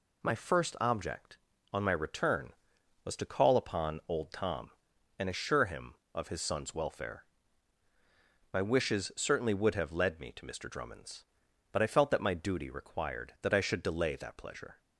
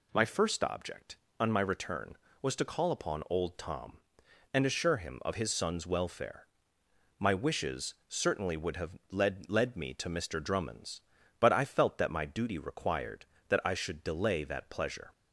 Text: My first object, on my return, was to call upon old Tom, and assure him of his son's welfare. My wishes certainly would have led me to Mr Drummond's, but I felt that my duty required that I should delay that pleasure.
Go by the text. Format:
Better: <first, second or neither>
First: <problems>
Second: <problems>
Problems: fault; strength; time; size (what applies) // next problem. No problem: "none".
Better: first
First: none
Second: says "led" twice; at 9.4 s